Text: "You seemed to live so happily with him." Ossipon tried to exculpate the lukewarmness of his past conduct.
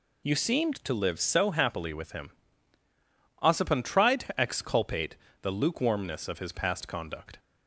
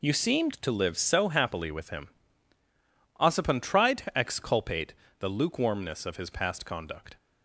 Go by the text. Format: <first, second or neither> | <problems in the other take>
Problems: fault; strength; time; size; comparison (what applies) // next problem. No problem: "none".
first | gets quieter; strong; throughout; 11.5 dB // pauses between "exculpate" and "the"; slight; at 4.9 s; 0.24 s long; slight in the first